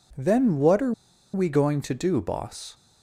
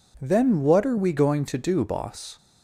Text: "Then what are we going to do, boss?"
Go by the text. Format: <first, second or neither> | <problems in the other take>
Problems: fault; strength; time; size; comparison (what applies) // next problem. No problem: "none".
second | pauses between "are" and "we"; at 0.9 s; 0.42 s long